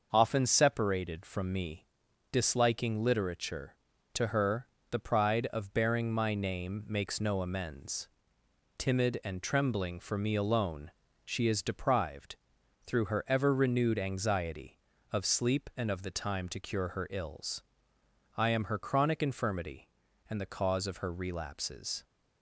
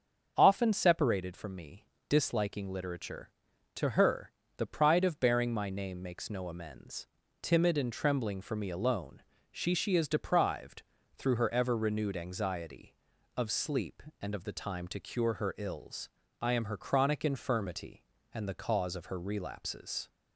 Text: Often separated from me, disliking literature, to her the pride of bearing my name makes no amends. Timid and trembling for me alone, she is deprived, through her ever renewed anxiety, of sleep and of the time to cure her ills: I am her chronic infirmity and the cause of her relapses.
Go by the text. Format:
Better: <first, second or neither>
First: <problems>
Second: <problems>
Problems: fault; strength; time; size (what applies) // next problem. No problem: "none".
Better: first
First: starts louder than the rest; noticeable; until 1.1 s; 6 dB // pauses between "her" and "the"; slight; at 4.6 s; 0.24 s long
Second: starts louder than the rest; until 1.3 s; 7 dB // pauses between "her" and "the"; slight; at 4.3 s; 0.26 s long // says "she" twice; at 9.7 s